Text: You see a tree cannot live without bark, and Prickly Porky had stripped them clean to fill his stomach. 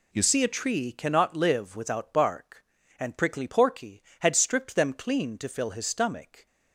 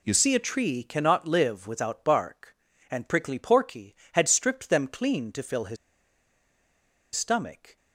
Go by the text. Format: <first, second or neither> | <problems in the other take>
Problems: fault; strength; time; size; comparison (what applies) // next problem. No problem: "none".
first | pauses between "his" and "stomach"; strong; at 5.7 s; 1.3 s long